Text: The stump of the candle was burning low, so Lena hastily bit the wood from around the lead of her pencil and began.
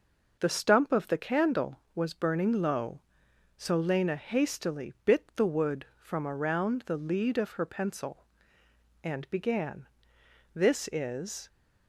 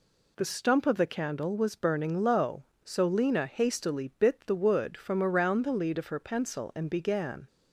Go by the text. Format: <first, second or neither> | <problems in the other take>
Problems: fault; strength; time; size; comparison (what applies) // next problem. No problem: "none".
second | goes on to say "This is"; noticeable; from 10.5 s on; 0.94 s long